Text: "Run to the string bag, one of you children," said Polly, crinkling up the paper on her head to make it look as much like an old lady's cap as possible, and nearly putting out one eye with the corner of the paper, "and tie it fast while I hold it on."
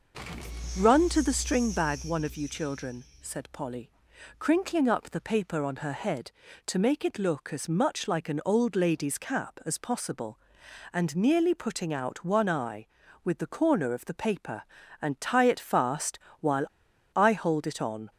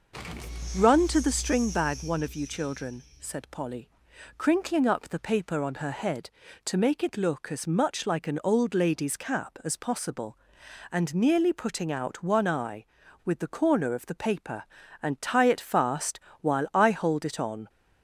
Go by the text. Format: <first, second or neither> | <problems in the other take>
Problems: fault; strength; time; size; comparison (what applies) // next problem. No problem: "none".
second | pauses between "fast" and "while"; slight; at 16.1 s; 0.22 s long; slight in the second // pauses between "while" and "I"; noticeable; at 16.6 s; 0.48 s long